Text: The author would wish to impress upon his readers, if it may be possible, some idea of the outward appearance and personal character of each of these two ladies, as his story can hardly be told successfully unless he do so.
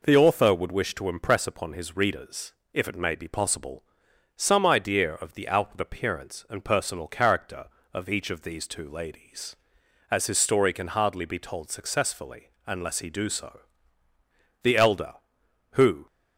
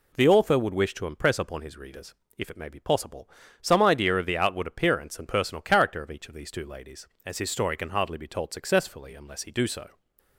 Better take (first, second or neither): second